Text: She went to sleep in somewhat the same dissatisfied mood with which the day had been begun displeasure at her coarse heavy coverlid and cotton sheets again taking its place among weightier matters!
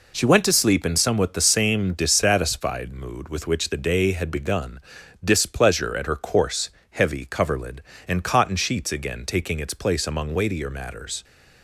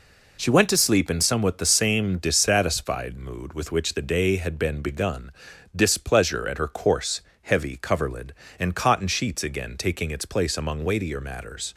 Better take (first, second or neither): second